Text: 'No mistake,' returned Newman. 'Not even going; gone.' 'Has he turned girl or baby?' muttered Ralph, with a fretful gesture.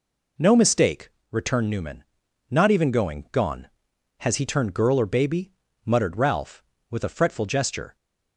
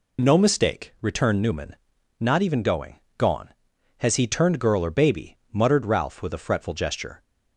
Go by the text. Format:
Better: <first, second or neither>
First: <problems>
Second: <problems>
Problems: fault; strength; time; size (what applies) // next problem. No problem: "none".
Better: neither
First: none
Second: none